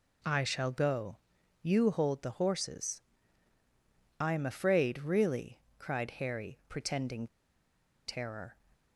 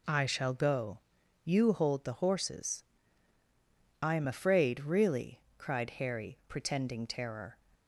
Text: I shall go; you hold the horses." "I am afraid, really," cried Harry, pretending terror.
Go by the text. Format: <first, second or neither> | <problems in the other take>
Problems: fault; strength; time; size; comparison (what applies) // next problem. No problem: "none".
second | pauses between "pretending" and "terror"; noticeable; at 7.2 s; 0.81 s long